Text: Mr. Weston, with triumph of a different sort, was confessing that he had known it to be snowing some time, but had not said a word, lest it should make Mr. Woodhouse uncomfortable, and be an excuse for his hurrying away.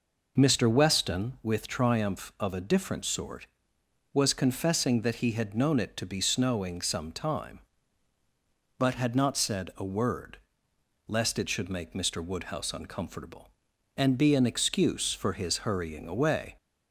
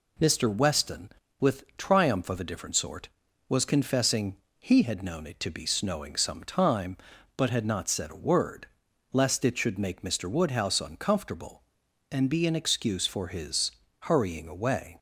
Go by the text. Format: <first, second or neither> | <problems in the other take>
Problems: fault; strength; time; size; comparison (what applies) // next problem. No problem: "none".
first | skips "that"; at 4.4 s // pauses between "his" and "hurrying"; slight; at 13.7 s; 0.30 s long